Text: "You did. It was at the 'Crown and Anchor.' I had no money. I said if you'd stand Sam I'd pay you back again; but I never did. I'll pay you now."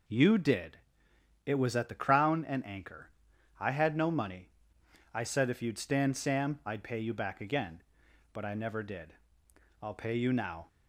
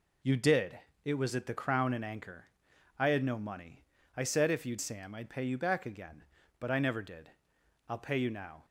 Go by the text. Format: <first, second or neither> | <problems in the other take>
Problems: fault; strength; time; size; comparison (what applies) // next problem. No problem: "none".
first | skips "stand"; at 4.8 s